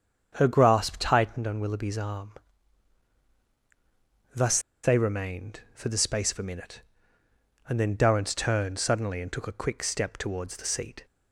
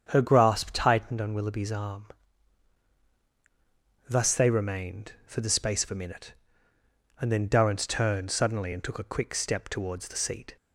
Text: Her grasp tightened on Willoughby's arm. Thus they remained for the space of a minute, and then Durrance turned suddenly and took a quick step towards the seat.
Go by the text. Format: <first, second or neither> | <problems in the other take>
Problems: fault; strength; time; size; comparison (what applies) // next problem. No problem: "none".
second | starts louder than the rest; strong; until 1.4 s; 7.5 dB; strong in the second // pauses between "Thus" and "they"; slight; at 4.5 s; 0.24 s long